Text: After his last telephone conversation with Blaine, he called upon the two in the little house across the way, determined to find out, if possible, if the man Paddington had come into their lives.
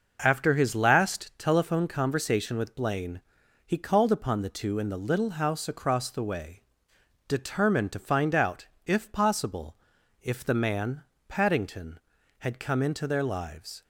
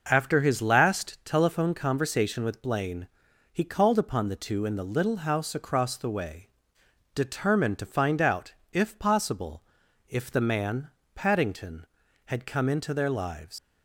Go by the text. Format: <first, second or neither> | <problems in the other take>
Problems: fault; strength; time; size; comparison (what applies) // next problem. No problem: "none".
first | pauses between "man" and "Paddington"; slight; at 10.9 s; 0.24 s long; slight in the first // leaves "lives" unfinished; at 13.5 s; 105 ms